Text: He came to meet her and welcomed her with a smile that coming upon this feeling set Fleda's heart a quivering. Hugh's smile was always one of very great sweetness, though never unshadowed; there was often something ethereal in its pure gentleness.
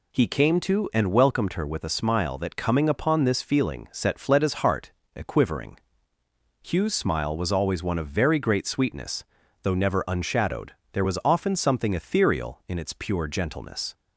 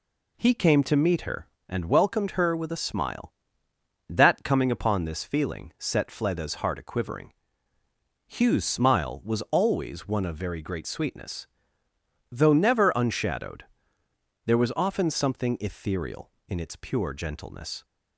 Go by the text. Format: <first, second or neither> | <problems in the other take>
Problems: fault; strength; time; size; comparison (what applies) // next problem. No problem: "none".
second | skips "meet her"; at 0.9 s // pauses between "heart" and "a"; slight; at 4.8 s; 0.24 s long